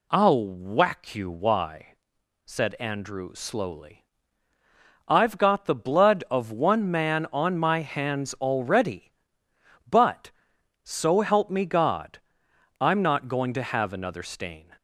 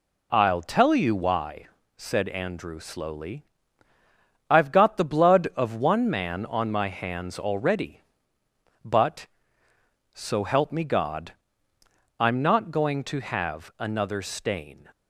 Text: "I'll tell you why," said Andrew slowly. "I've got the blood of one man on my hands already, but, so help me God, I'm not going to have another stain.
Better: second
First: says "whack" for "tell"; at 0.4 s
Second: none

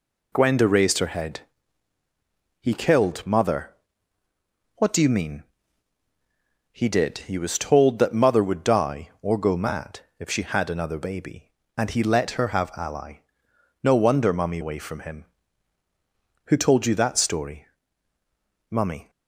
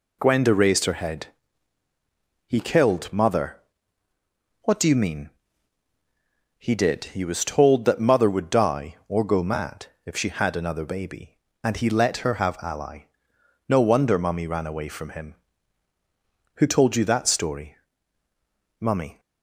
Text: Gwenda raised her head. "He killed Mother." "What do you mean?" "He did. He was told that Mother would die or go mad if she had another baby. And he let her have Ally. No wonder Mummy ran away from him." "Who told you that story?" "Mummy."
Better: second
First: pauses between "mad" and "if"; slight; at 10.0 s; 0.18 s long // skips "ran"; at 14.6 s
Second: pauses between "mad" and "if"; slight; at 9.8 s; 0.18 s long

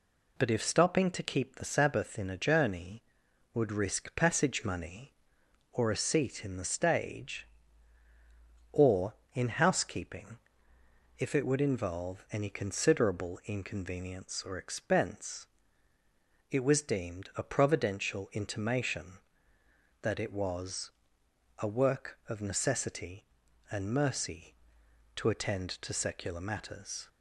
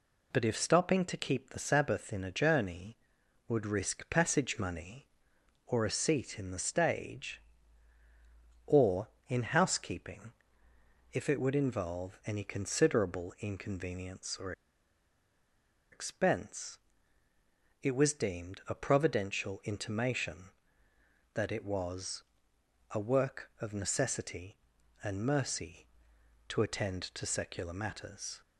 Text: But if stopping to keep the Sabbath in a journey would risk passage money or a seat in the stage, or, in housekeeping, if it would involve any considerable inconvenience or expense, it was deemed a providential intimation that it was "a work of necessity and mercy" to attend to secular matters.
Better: first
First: pauses between "was" and "a"; noticeable; at 20.9 s; 0.70 s long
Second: pauses between "or" and "expense"; strong; at 14.5 s; 1.4 s long // pauses between "was" and "a"; noticeable; at 22.2 s; 0.70 s long

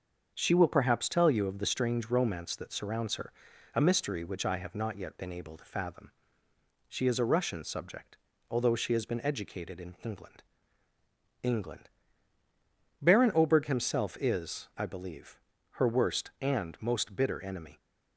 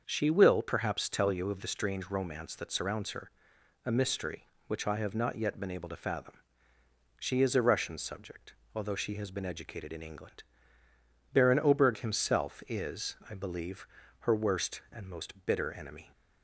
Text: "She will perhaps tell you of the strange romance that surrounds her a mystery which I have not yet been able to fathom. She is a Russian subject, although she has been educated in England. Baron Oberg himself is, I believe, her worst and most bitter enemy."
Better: second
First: starts louder than the rest; until 1.3 s; 7 dB // pauses between "her" and "a"; at 3.3 s; 0.44 s long // says "England" twice; at 11.4 s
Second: starts louder than the rest; until 1.0 s; 6.5 dB // pauses between "her" and "a"; noticeable; at 3.3 s; 0.52 s long

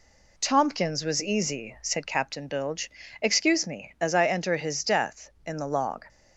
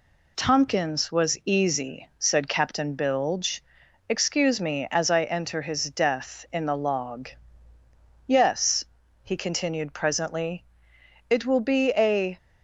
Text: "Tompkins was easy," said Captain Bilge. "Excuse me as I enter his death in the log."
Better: first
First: none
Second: goes on to say "Yes he continued presently it will be a"; strong; from 8.2 s on; 4.1 s long

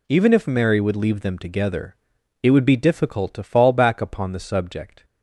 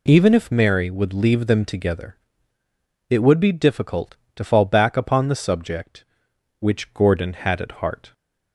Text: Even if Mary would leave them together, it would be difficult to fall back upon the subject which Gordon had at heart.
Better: second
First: stops before "which Gordon had at heart"; at 5.0 s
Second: none

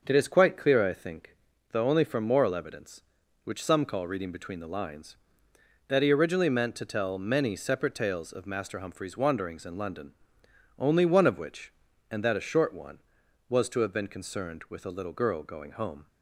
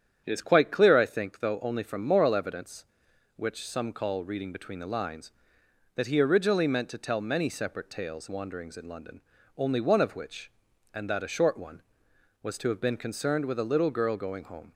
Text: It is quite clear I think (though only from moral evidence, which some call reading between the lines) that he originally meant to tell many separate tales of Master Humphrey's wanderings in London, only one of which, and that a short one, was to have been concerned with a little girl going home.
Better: first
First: starts louder than the rest; until 1.0 s; 6.5 dB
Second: starts louder than the rest; strong; until 1.2 s; 9 dB // skips "of Master Humphrey's"; at 8.2 s

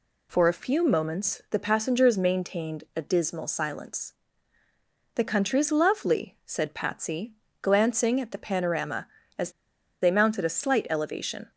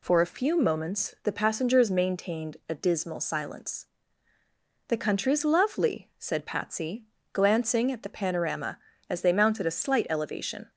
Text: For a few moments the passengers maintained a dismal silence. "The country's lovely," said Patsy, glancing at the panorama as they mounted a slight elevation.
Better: second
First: pauses between "as" and "they"; noticeable; at 9.5 s; 0.51 s long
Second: none

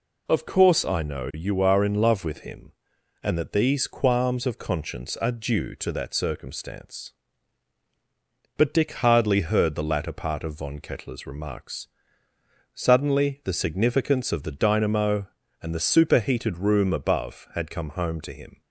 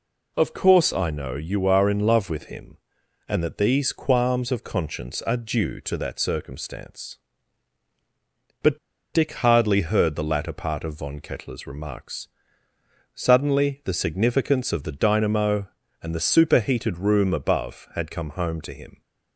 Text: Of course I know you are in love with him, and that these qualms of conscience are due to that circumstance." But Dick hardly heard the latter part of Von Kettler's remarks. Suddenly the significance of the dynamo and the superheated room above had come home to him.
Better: first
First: none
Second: pauses between "But" and "Dick"; slight; at 8.7 s; 0.35 s long

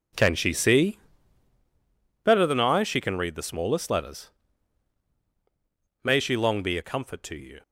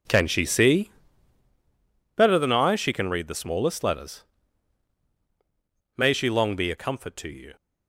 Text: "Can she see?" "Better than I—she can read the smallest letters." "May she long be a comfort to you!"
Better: neither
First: none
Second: none

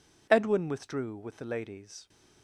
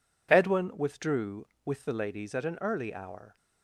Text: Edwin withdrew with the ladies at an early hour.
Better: second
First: stops before "at an early hour"; at 2.0 s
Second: none

